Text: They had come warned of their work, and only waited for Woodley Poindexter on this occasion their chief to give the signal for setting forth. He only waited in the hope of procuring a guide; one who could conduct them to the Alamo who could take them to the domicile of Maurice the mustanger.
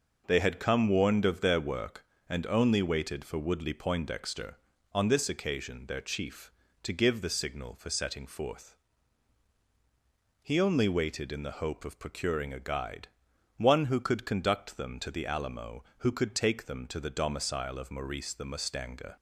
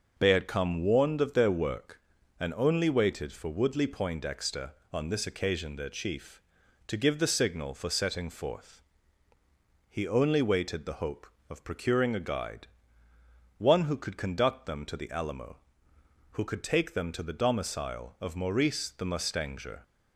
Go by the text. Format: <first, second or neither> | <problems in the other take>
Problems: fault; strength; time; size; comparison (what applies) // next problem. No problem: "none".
first | skips "in"; at 10.8 s